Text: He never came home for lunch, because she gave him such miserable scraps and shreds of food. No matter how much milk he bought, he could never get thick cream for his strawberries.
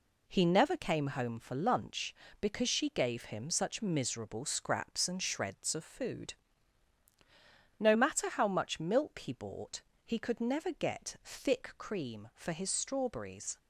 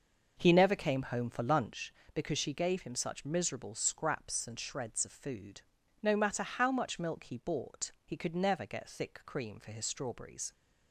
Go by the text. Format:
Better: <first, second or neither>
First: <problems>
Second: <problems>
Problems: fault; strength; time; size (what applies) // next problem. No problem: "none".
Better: first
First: none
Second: starts louder than the rest; noticeable; until 1.8 s; 6 dB